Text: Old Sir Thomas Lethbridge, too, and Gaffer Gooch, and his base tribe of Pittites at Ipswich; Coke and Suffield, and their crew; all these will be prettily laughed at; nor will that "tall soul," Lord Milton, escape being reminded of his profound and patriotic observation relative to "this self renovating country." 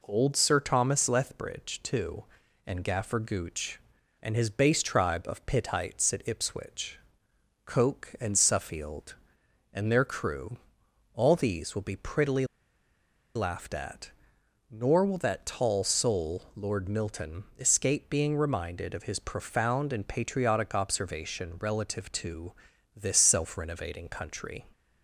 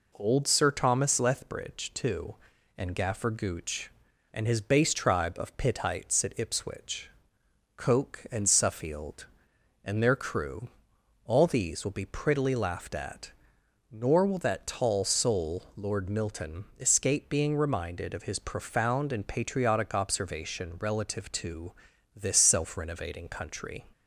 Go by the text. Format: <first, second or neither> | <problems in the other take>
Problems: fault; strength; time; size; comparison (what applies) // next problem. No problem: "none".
second | pauses between "prettily" and "laughed"; noticeable; at 12.4 s; 0.91 s long // pauses between "to" and "this"; noticeable; at 22.5 s; 0.46 s long; noticeable in the second